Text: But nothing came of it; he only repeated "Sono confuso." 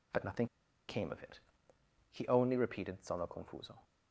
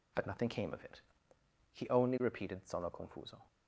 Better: second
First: pauses between "nothing" and "came"; at 0.4 s; 0.43 s long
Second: none

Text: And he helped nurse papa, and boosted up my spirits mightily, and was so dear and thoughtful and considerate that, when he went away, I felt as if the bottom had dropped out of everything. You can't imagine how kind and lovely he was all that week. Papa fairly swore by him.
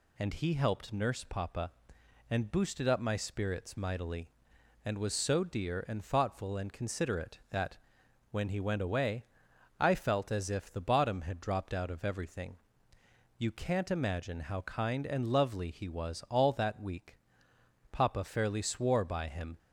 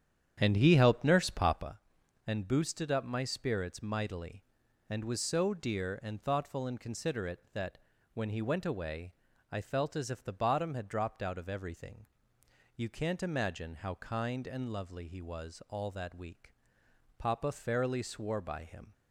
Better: first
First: none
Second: starts louder than the rest; strong; until 1.7 s; 9 dB

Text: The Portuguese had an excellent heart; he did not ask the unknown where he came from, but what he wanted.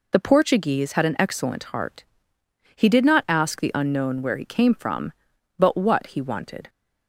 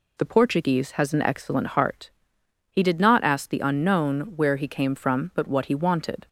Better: first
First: none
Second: says "has" for "had"; at 0.9 s

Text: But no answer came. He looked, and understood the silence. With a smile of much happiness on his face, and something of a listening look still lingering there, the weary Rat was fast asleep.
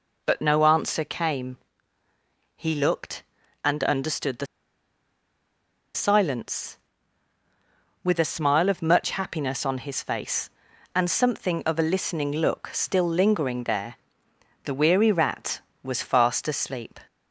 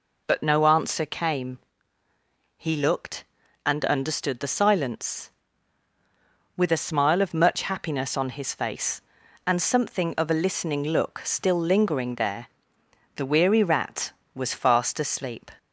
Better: second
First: pauses between "the" and "silence"; strong; at 4.4 s; 1.4 s long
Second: none

